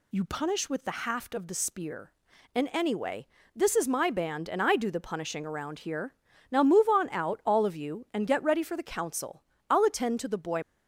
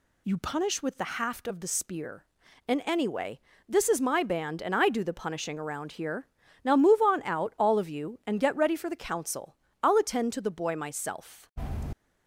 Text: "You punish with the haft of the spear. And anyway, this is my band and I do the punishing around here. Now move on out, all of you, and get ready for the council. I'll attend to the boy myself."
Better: second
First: stops before "myself"; at 10.6 s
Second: none

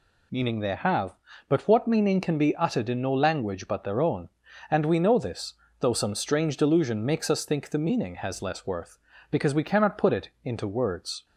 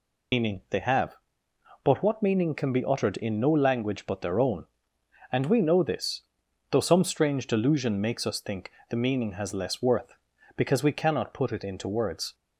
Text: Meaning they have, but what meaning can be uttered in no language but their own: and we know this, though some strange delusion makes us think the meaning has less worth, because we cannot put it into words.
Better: first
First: none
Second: loses the start of "Meaning"; at 0.3 s; 95 ms // pauses between "think" and "the"; slight; at 8.7 s; 0.18 s long

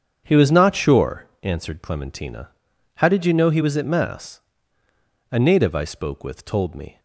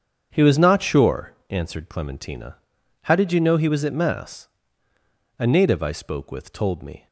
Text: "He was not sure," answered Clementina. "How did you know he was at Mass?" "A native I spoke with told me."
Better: neither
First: starts louder than the rest; strong; until 1.2 s; 7.5 dB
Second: starts louder than the rest; strong; until 1.3 s; 7.5 dB

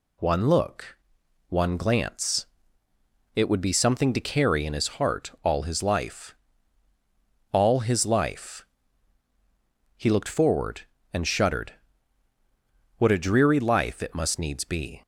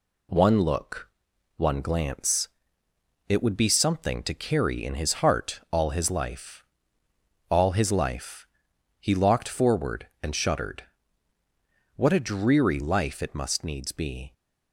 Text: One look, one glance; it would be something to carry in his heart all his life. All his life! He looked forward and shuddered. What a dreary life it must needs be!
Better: first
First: none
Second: says "locked" for "looked"; at 9.1 s

